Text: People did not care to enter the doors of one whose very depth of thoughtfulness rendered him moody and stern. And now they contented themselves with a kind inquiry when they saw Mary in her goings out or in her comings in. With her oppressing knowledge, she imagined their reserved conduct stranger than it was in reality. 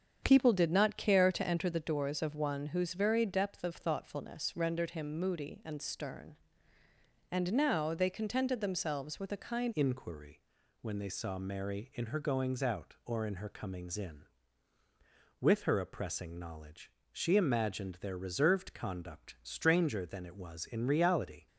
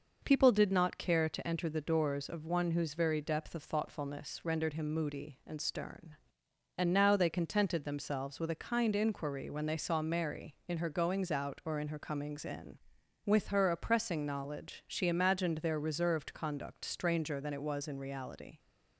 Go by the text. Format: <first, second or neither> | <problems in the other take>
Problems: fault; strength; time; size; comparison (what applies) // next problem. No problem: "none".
second | starts louder than the rest; strong; until 1.2 s; 7.5 dB // changes voice at "inquiry"; from 9.7 s on; 11.7 s long // pauses between "inquiry" and "when"; at 10.4 s; 0.40 s long